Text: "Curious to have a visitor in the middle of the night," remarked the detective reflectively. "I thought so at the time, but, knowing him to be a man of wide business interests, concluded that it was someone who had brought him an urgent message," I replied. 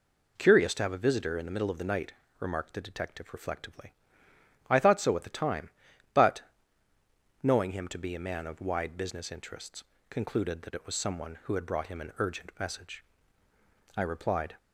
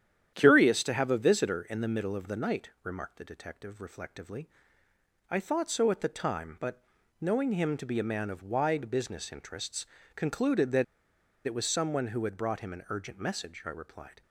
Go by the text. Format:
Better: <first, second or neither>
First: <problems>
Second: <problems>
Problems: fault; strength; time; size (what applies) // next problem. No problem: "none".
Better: first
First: none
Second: starts louder than the rest; strong; until 1.3 s; 10 dB // pauses between "that" and "it"; noticeable; at 10.8 s; 0.62 s long